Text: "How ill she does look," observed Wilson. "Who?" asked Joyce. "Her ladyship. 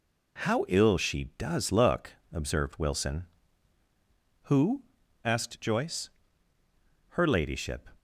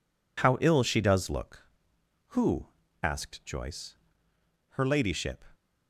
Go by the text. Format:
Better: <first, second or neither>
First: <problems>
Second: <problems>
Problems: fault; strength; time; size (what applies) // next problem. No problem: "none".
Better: first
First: none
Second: skips "observed Wilson"; at 2.0 s